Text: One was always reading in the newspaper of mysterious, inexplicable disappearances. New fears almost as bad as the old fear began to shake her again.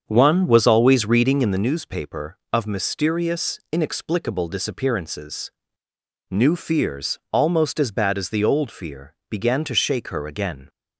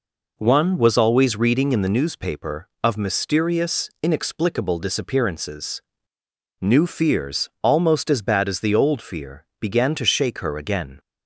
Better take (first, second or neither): second